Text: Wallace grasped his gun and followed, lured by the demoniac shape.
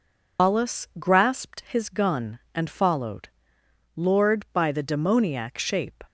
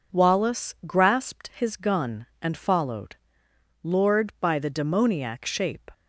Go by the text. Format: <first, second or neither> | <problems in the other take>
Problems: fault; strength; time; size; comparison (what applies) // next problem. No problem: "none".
second | loses the start of "Wallace"; at 0.3 s; 150 ms